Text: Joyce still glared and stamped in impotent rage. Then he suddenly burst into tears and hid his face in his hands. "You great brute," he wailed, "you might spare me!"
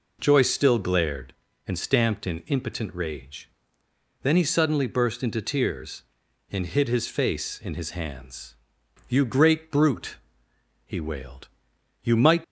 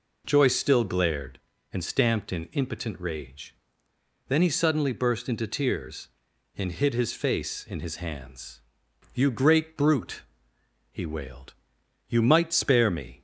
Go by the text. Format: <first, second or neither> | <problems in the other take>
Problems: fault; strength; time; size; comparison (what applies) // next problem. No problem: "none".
second | stops before "spare me"; at 12.4 s